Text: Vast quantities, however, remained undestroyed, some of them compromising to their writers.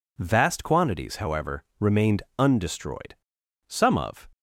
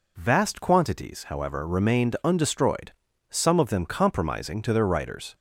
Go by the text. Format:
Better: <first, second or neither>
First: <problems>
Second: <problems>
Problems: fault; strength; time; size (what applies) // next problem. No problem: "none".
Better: second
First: pauses between "remained" and "undestroyed"; slight; at 2.2 s; 0.16 s long // stops before "them compromising to their writers"; at 4.3 s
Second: none